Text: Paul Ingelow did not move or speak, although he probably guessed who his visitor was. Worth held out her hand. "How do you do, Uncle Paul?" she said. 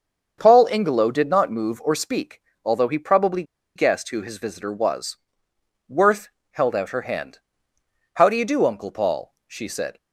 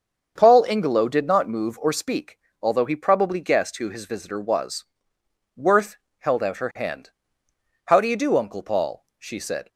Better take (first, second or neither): second